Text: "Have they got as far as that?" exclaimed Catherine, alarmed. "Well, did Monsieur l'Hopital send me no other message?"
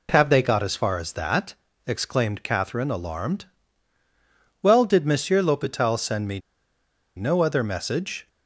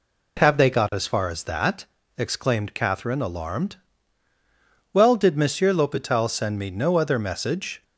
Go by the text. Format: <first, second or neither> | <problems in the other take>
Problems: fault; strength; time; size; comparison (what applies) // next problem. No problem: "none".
second | pauses between "me" and "no"; noticeable; at 6.3 s; 0.76 s long